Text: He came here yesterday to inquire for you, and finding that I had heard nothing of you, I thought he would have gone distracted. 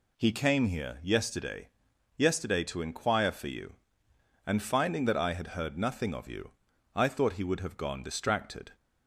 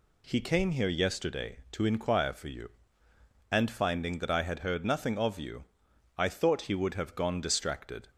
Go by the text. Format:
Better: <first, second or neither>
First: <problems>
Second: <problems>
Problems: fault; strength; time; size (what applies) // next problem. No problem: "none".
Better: second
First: says "yesterday" twice; at 2.1 s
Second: none